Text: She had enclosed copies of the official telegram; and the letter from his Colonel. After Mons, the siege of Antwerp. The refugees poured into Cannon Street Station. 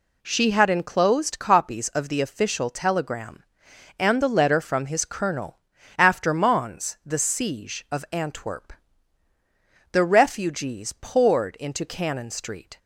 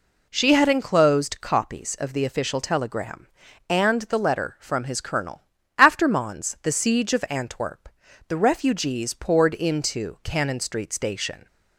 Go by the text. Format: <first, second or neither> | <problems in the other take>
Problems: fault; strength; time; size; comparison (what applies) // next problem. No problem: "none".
second | stops before "Station"; at 12.7 s